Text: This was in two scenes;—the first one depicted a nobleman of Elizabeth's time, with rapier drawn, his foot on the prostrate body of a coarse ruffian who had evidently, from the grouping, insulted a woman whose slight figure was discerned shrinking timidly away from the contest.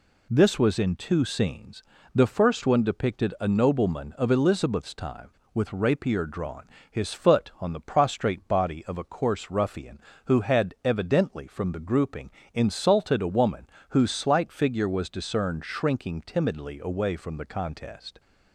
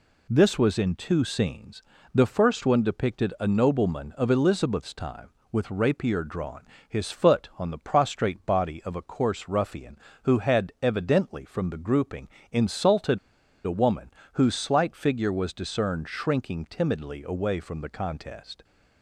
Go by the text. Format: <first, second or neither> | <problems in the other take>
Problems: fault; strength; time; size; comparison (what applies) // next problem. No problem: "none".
first | pauses between "insulted" and "a"; noticeable; at 13.1 s; 0.48 s long // pauses between "woman" and "whose"; slight; at 14.0 s; 0.22 s long; slight in the first